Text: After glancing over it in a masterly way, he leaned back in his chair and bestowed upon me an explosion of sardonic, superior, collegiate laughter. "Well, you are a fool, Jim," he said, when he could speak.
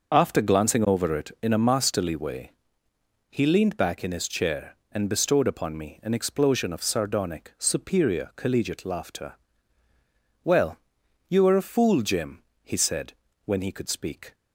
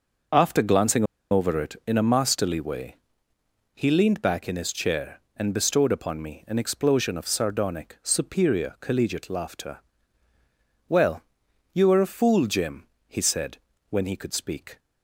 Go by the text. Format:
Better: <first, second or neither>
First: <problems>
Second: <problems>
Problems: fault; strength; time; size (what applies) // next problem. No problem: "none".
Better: first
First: none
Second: pauses between "glancing" and "over"; slight; at 1.0 s; 0.27 s long